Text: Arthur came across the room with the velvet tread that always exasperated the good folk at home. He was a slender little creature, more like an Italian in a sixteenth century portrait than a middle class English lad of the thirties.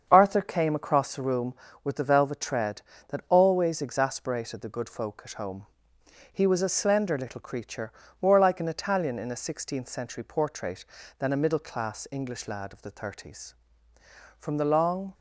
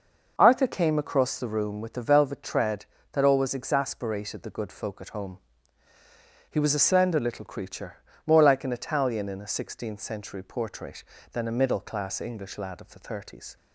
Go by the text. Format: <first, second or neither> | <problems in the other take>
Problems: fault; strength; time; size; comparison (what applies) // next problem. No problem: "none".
second | starts louder than the rest; strong; until 1.1 s; 7 dB // goes on to say "From the long"; noticeable; from 14.3 s on; 0.76 s long